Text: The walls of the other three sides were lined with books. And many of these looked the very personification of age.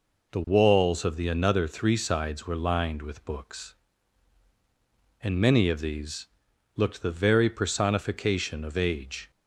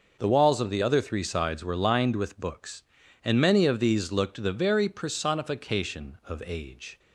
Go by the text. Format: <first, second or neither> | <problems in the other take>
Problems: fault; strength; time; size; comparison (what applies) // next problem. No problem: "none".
second | says "another" for "other"; at 1.2 s // pauses between "these" and "looked"; noticeable; at 6.2 s; 0.48 s long